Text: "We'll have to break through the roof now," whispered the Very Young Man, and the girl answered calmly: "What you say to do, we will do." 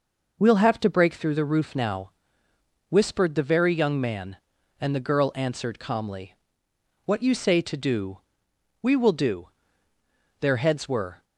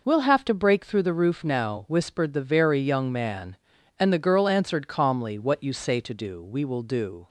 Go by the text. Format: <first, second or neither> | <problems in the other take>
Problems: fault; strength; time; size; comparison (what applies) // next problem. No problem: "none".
second | goes on to say "Their heads were"; noticeable; from 10.4 s on; 0.82 s long